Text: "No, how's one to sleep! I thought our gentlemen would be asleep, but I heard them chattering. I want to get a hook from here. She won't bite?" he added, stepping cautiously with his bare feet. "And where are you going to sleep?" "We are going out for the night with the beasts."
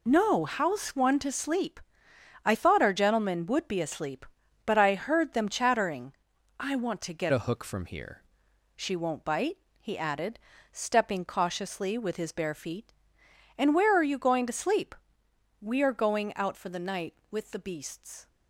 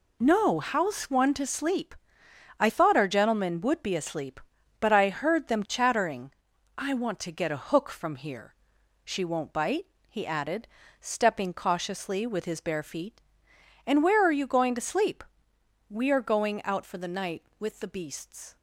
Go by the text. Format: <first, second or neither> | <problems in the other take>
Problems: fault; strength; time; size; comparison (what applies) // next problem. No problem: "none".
second | changes voice from "a" to "here"; from 7.3 to 8.2 s; 0.9 s long